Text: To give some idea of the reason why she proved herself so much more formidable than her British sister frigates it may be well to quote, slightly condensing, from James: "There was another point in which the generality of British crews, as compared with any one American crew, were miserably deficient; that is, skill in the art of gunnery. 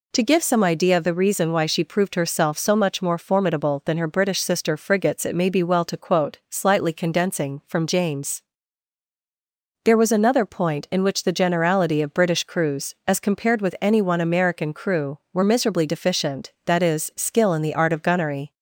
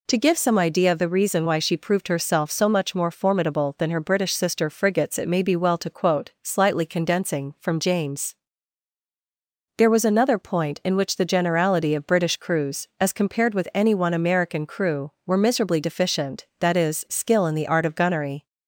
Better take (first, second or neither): neither